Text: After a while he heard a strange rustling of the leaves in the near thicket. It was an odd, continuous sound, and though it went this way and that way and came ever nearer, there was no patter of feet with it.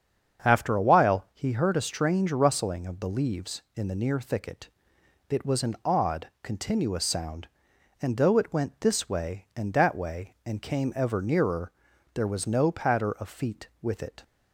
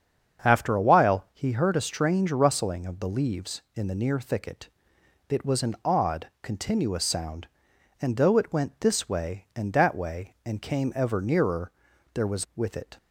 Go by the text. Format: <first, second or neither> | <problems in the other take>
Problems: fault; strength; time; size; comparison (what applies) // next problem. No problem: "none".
first | starts louder than the rest; strong; until 1.5 s; 7.5 dB; strong in the first // skips "no patter of feet"; at 12.5 s